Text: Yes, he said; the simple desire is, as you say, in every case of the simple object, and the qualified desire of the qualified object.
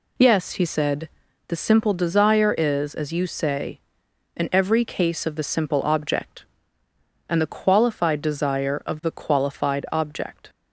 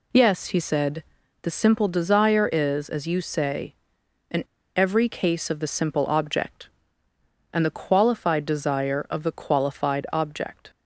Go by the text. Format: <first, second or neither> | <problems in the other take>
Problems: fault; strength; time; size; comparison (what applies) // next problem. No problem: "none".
first | pauses between "in" and "every"; slight; at 4.4 s; 0.33 s long